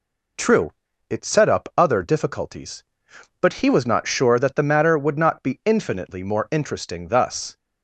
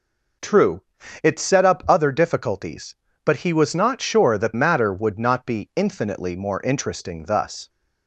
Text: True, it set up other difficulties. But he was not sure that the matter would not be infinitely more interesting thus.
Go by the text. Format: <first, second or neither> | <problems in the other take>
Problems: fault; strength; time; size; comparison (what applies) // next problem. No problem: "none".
first | skips "the"; at 4.5 s